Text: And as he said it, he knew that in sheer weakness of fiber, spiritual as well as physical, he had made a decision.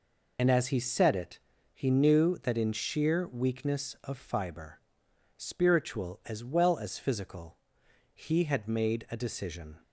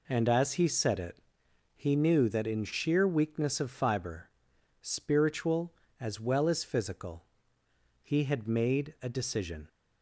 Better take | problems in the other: second | loses the start of "And"; at 0.3 s; 75 ms

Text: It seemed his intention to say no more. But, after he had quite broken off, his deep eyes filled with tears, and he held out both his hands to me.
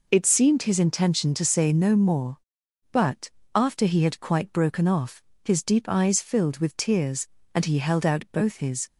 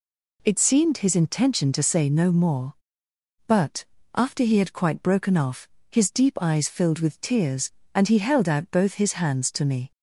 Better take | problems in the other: second | stops before "hands to me"; at 8.8 s

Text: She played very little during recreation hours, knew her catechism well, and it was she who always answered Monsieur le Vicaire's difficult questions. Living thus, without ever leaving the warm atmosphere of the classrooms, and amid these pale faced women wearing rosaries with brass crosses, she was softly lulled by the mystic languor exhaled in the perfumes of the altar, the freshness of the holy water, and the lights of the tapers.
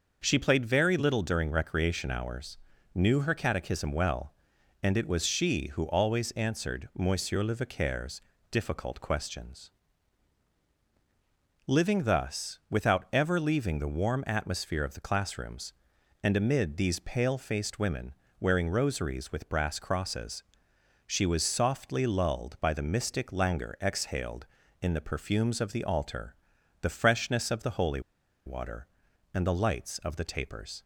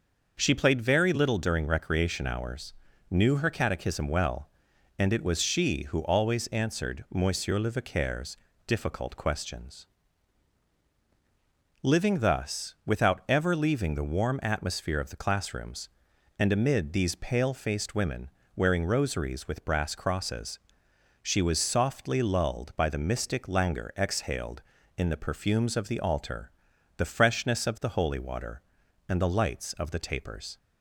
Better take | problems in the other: second | starts louder than the rest; noticeable; until 1.2 s; 6 dB; noticeable in the second // pauses between "Vicaire's" and "difficult"; slight; at 8.2 s; 0.32 s long; slight in the second // pauses between "women" and "wearing"; slight; at 18.1 s; 0.24 s long; slight in the second // pauses between "holy" and "water"; at 28.0 s; 0.45 s long

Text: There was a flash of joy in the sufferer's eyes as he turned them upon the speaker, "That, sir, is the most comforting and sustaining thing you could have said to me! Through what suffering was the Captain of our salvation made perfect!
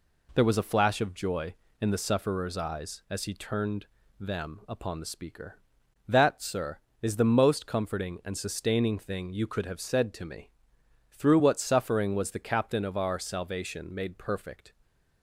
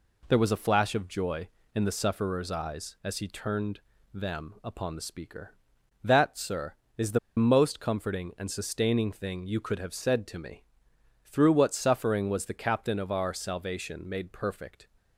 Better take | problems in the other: first | pauses between "turned" and "them"; slight; at 3.7 s; 0.34 s long; slight in the first // pauses between "the" and "most"; slight; at 7.1 s; 0.18 s long

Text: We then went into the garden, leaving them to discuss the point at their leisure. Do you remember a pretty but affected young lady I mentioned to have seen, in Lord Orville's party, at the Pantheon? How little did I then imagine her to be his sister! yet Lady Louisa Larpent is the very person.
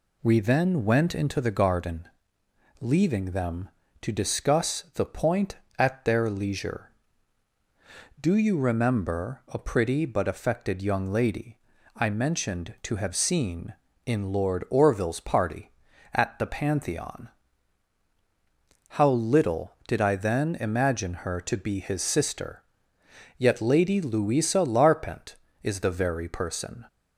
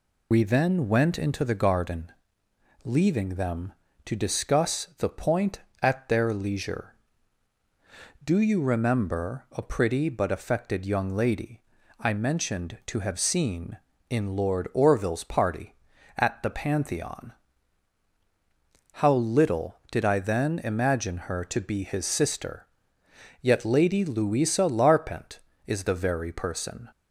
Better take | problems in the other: first | loses the start of "We"; at 0.3 s; 60 ms // pauses between "lady" and "I"; at 11.6 s; 0.38 s long; also in the first

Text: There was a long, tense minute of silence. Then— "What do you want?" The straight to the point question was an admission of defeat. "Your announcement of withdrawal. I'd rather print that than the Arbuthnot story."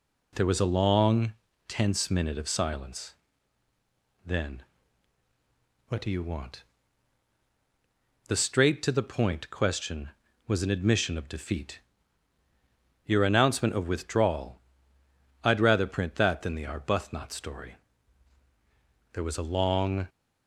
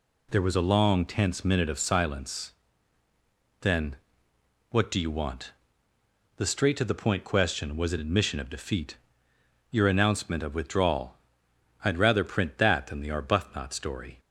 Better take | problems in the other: second | goes on to say "There was a long"; noticeable; from 19.1 s on; 0.96 s long

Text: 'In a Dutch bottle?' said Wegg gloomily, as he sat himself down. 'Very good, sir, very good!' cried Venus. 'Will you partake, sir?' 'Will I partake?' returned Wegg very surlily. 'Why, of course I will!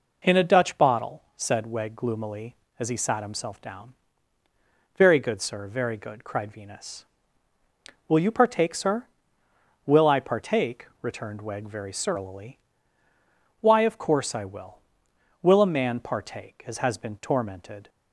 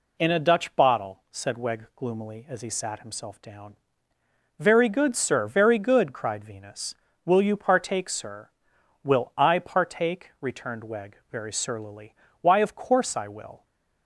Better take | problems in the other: second | goes on to say "WILL a man partake as has been tormented"; strong; from 15.4 s on; 2.4 s long

